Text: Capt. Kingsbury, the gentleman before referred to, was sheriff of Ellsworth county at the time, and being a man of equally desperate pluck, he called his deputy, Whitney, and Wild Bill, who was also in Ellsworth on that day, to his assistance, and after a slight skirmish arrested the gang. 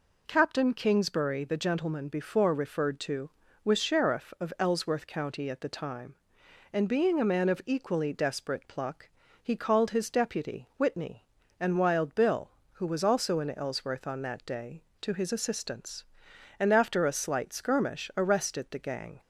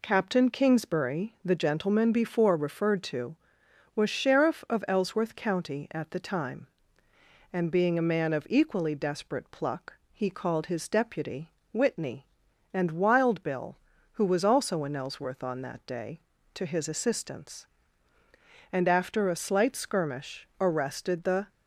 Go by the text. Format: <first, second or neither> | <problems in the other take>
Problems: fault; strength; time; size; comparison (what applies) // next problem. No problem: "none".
first | stops before "gang"; at 21.4 s